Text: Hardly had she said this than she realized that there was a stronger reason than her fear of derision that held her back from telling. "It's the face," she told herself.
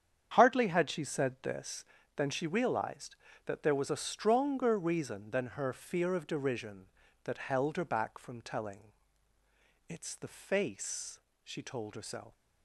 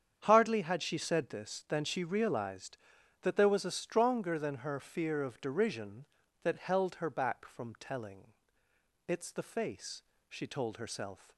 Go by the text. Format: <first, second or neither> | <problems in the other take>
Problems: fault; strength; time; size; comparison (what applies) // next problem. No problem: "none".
first | starts louder than the rest; strong; until 1.2 s; 8 dB; strong in the first // skips "reason"; at 4.3 s